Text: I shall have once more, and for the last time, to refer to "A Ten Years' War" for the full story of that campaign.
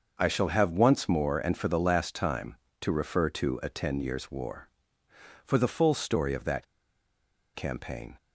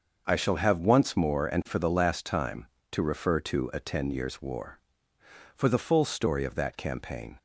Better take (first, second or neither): second